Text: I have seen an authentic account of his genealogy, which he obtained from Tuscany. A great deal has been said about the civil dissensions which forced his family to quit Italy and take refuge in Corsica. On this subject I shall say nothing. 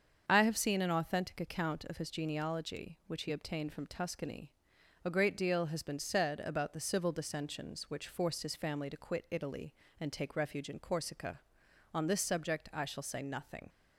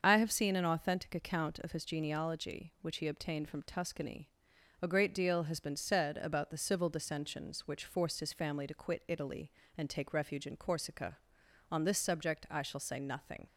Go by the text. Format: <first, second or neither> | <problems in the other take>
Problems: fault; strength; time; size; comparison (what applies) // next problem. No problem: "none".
neither | starts louder than the rest; the same in both